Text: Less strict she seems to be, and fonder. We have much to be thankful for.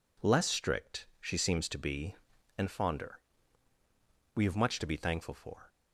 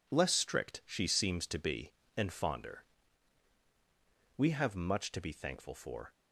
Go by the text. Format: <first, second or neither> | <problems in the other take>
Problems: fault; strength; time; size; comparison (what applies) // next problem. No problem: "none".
neither | none